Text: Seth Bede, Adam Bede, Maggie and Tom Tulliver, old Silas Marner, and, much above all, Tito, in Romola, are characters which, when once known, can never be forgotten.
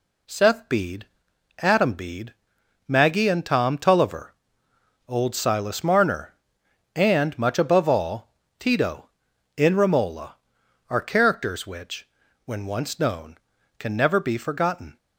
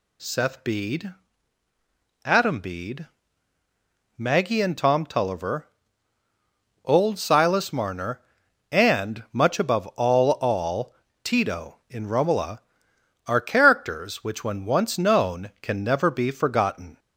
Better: first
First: none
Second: says "all" twice; at 10.3 s

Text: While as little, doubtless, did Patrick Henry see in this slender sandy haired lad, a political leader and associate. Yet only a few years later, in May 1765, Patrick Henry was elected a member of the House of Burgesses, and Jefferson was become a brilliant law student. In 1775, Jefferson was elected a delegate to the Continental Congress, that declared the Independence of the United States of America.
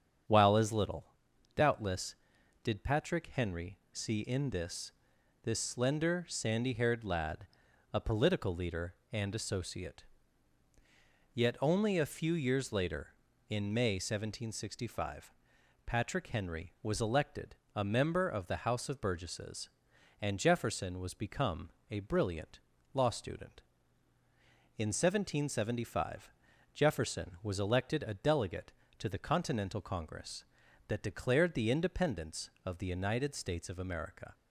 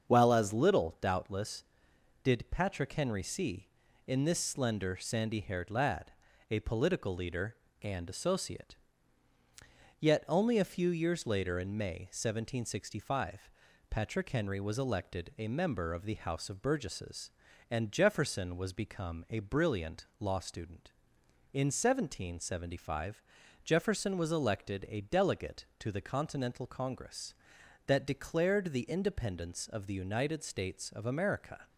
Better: second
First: starts louder than the rest; strong; until 1.7 s; 8 dB // pauses between "Henry" and "see"; slight; at 3.7 s; 0.16 s long // says "this" twice; at 5.4 s // pauses between "elected" and "a"; slight; at 17.5 s; 0.18 s long // pauses between "become" and "a"; slight; at 21.6 s; 0.20 s long // pauses between "brilliant" and "law"; slight; at 22.5 s; 0.34 s long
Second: starts louder than the rest; strong; until 1.1 s; 7 dB

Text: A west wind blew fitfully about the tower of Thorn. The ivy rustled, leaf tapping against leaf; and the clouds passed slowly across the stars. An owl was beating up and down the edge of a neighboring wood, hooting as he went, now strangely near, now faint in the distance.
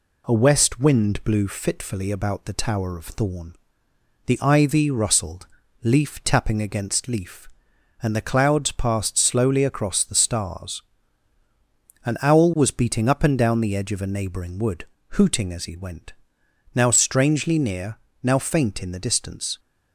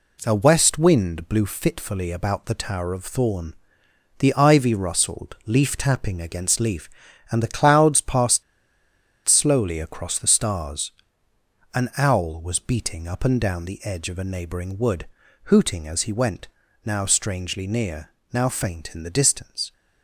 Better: first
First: none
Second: pauses between "passed" and "slowly"; noticeable; at 8.4 s; 0.82 s long

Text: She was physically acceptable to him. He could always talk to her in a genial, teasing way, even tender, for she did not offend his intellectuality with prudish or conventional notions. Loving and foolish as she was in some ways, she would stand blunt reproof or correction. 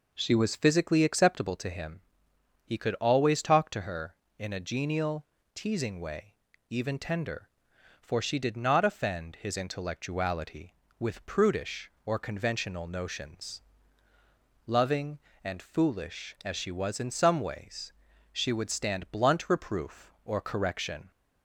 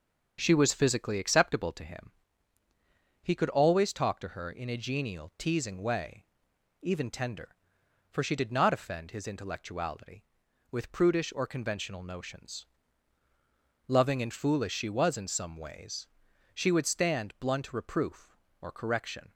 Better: first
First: none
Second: starts louder than the rest; until 1.4 s; 7 dB // skips "as"; at 14.7 s

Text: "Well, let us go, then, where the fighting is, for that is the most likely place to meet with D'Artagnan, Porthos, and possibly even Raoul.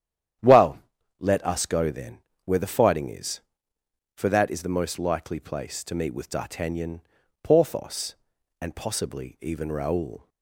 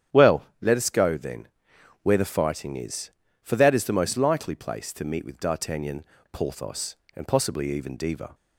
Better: first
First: starts louder than the rest; strong; until 1.8 s; 10 dB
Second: starts louder than the rest; strong; until 1.3 s; 9.5 dB // says "Diva" for "Raoul"; at 7.9 s

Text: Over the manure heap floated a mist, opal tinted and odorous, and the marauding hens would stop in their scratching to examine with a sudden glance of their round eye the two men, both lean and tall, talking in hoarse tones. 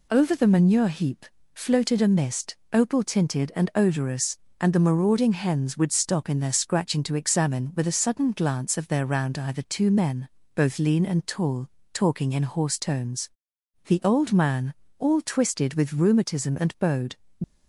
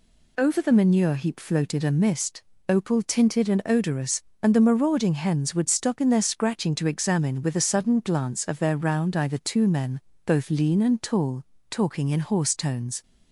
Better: second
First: pauses between "heap" and "floated"; slight; at 1.2 s; 0.30 s long // goes on to say "The old man all twisted with rheumatism and bowed"; strong; from 13.8 s on; 3.2 s long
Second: none

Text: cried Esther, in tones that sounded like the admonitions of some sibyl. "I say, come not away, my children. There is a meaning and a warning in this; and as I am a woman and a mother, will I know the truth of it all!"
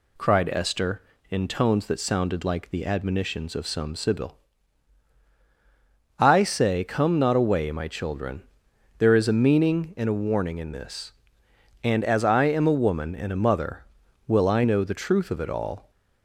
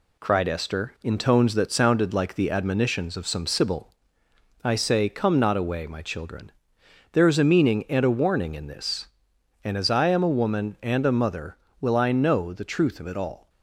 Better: first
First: none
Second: gets quieter; throughout; 3.5 dB

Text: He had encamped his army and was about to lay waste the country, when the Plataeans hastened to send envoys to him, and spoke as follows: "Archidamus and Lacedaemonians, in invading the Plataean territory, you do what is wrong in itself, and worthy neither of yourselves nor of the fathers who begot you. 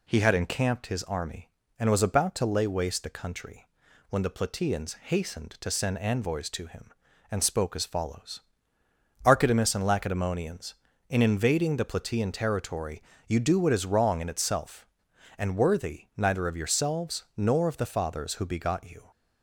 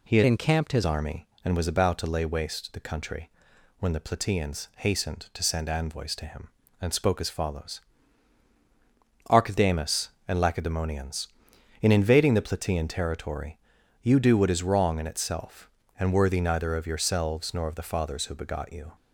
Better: first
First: none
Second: changes voice from "encamped" to "his"; from 0.2 to 0.8 s; 0.6 s long

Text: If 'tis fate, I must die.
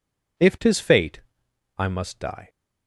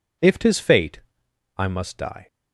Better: neither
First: none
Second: none

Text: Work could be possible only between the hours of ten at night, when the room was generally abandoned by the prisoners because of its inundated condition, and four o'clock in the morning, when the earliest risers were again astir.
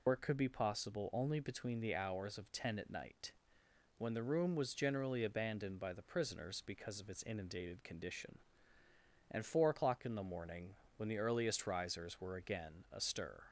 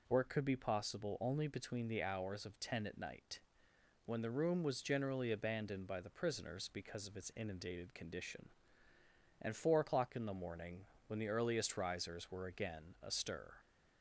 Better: second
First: loses the start of "Work"; at 0.0 s; 70 ms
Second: none

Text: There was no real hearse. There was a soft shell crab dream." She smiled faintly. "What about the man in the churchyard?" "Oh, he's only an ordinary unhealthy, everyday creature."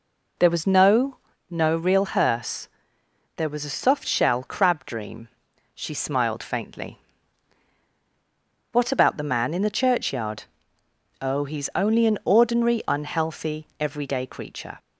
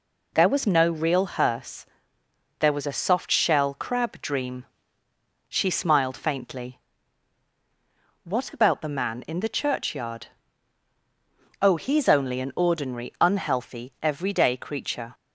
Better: second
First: says "no" twice; at 1.5 s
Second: none

